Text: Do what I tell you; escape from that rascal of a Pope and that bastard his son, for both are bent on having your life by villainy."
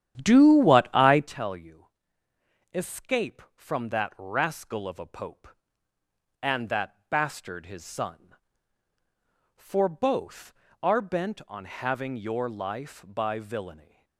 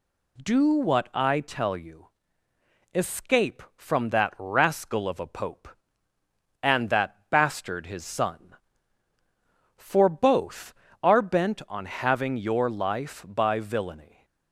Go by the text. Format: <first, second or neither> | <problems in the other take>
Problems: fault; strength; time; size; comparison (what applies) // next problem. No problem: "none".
second | starts louder than the rest; strong; until 1.4 s; 10.5 dB